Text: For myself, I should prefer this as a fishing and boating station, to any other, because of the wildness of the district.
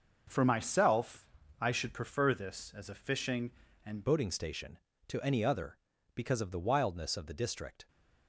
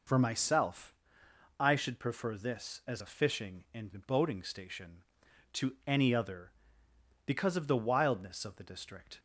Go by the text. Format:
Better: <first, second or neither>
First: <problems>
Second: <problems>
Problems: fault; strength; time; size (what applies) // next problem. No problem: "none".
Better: second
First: changes voice at "boating"; from 4.0 s on; 3.8 s long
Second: none